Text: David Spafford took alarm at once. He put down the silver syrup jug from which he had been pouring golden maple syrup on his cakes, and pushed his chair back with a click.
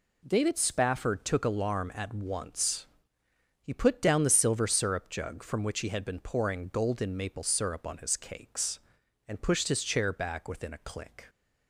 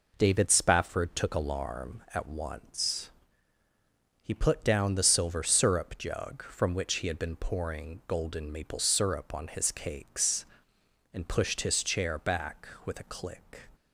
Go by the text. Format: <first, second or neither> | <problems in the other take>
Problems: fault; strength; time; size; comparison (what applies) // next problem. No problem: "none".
second | says "within" for "with"; at 10.4 s